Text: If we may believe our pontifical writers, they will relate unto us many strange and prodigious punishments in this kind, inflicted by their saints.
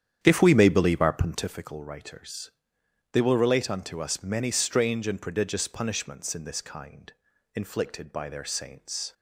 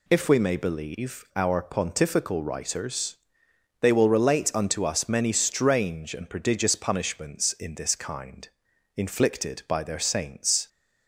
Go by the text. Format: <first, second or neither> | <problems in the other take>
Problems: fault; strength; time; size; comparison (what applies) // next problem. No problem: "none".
second | starts louder than the rest; strong; until 1.6 s; 9.5 dB